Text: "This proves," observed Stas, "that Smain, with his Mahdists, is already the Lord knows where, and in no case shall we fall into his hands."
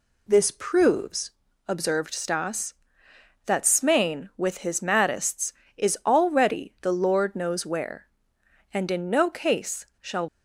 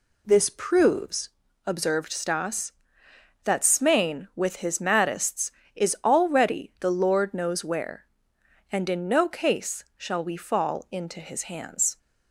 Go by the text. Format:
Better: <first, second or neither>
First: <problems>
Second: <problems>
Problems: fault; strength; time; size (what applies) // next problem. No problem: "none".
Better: second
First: stops before "we fall into his hands"; at 10.2 s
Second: none